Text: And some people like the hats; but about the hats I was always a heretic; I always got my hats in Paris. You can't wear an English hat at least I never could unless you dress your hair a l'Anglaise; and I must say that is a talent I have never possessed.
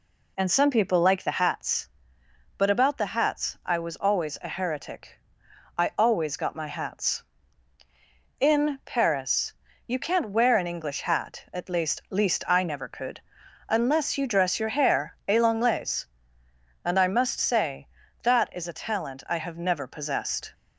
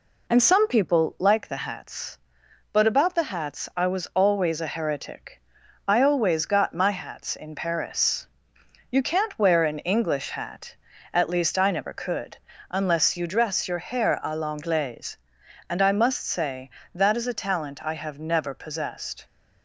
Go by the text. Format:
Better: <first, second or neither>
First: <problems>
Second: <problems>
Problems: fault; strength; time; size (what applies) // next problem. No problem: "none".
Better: second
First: says "least" twice; at 12.0 s // pauses between "could" and "unless"; noticeable; at 13.2 s; 0.48 s long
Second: pauses between "could" and "unless"; slight; at 12.3 s; 0.34 s long